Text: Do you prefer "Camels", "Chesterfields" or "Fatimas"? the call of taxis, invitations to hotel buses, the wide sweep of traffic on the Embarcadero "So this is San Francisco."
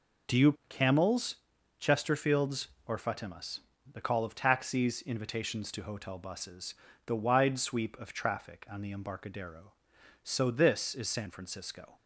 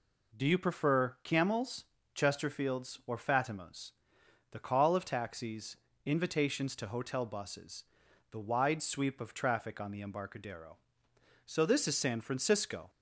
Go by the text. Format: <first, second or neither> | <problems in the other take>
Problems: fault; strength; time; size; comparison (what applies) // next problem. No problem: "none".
second | skips "prefer"; at 0.6 s